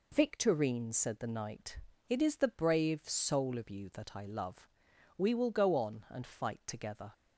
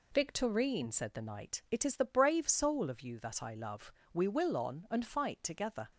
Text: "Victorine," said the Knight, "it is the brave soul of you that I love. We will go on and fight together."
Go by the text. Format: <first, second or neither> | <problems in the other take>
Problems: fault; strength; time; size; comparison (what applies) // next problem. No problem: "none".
first | skips "go"; at 4.5 s